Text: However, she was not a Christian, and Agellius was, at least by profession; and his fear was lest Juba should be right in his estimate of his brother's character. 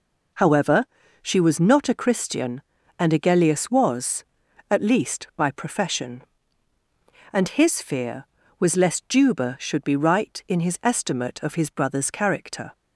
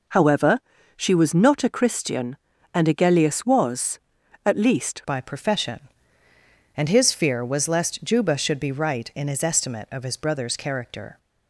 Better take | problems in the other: first | changes voice at "by"; from 5.0 s on; 6.1 s long

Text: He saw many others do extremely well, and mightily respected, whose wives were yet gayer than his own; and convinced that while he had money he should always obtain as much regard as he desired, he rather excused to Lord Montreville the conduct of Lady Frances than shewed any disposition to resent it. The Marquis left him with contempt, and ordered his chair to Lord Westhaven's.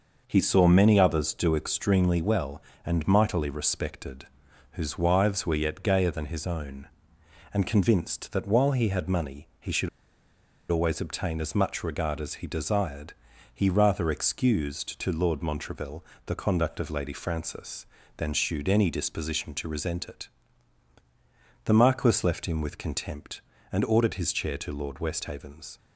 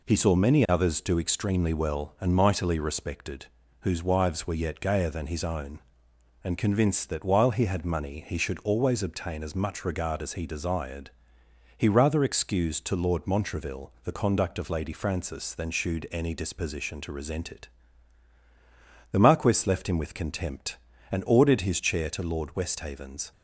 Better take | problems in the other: second | pauses between "should" and "always"; noticeable; at 9.8 s; 0.82 s long // pauses between "Montreville" and "the"; slight; at 16.0 s; 0.22 s long

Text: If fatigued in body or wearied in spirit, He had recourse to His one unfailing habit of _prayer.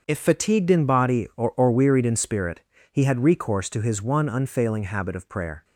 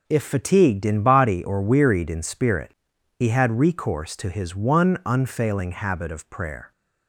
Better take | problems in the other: second | starts louder than the rest; until 1.0 s; 6.5 dB // says "or" twice; at 1.5 s

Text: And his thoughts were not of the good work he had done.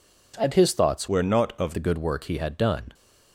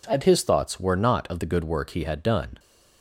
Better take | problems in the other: second | changes voice from "were" to "of"; from 1.0 to 1.7 s; 0.7 s long

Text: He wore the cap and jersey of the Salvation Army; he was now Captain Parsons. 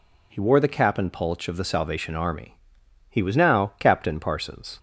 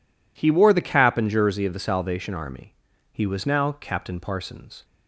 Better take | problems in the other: second | says "pulch" for "jersey"; at 1.1 s

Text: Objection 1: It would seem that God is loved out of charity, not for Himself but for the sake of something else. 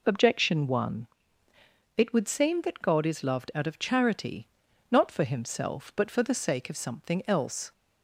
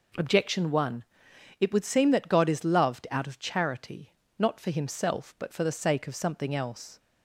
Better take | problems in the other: neither | none

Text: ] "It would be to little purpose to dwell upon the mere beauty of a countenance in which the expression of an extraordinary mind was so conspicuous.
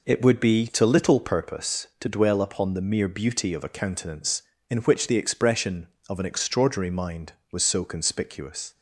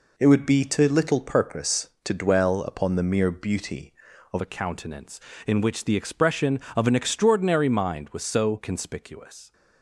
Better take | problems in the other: first | changes voice at "a"; from 4.4 s on; 5.1 s long

